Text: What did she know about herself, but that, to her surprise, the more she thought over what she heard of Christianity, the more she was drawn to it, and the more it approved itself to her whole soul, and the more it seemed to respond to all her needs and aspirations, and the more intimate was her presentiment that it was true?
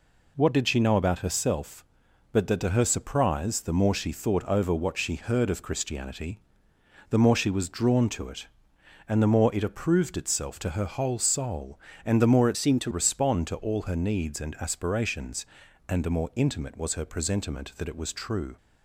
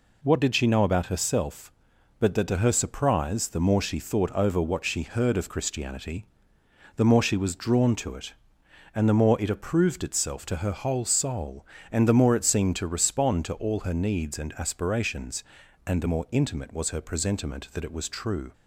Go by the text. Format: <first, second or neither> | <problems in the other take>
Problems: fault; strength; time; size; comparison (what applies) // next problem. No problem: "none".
second | changes voice from "seemed" to "to"; from 12.5 to 12.9 s; 0.4 s long